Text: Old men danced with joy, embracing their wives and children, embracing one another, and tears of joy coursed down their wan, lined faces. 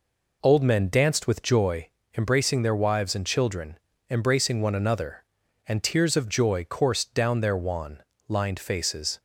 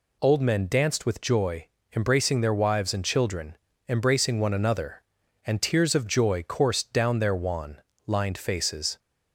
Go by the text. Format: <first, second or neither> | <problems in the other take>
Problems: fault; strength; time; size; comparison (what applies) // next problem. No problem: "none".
second | starts louder than the rest; noticeable; until 2.0 s; 4 dB